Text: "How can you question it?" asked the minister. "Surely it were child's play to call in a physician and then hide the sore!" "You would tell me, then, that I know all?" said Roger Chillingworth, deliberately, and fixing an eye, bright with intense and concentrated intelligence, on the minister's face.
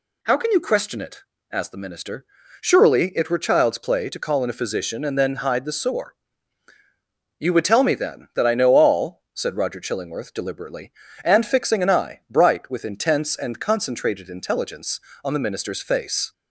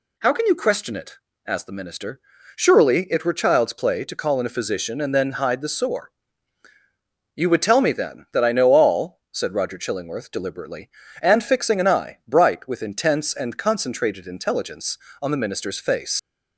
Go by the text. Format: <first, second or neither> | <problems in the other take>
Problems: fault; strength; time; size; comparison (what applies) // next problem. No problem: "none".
first | leaves "face" unfinished; at 16.1 s; 105 ms